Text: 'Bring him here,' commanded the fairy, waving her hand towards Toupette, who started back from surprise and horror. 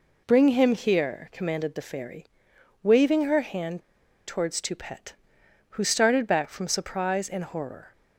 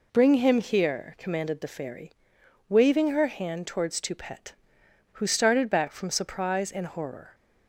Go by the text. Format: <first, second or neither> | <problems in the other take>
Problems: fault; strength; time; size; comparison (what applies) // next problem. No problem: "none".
second | pauses between "hand" and "towards"; noticeable; at 3.8 s; 0.47 s long